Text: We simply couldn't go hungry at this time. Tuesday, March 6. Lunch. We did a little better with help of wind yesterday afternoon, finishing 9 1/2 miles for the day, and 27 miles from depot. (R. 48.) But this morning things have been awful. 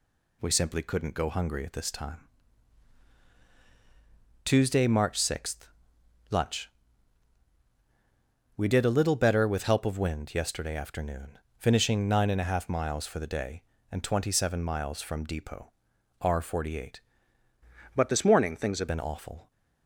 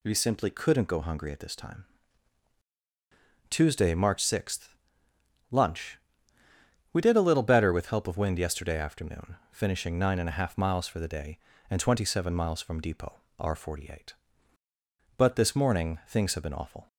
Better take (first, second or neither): second